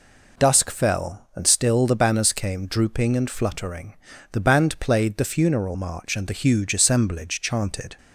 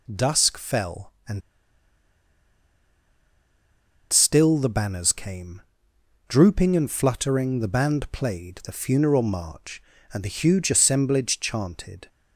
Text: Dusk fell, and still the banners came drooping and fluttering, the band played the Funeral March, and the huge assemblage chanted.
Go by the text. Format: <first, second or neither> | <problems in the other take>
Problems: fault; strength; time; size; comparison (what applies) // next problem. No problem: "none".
first | pauses between "and" and "still"; strong; at 1.4 s; 2.7 s long // pauses between "came" and "drooping"; noticeable; at 5.6 s; 0.66 s long